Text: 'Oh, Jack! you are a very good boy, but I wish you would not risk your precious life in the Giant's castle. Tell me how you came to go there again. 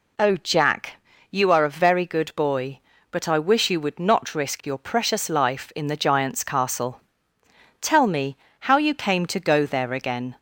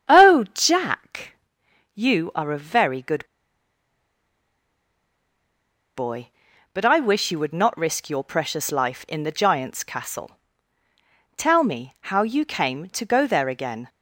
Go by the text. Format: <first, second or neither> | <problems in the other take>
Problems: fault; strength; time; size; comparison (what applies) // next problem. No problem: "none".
first | starts louder than the rest; strong; until 1.2 s; 8.5 dB // pauses between "good" and "boy"; strong; at 3.2 s; 2.7 s long // pauses between "me" and "how"; slight; at 11.9 s; 0.16 s long; slight in the first